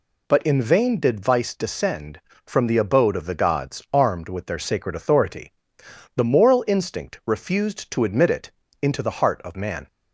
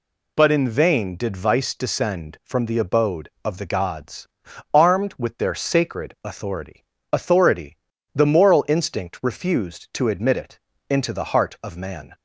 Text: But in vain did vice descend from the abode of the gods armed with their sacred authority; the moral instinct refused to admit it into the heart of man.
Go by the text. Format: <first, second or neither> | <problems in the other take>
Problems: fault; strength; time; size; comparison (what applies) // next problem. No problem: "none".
first | pauses between "gods" and "armed"; noticeable; at 4.2 s; 0.46 s long // says "authority" twice; at 7.1 s // pauses between "it" and "into"; slight; at 10.5 s; 0.30 s long; slight in the first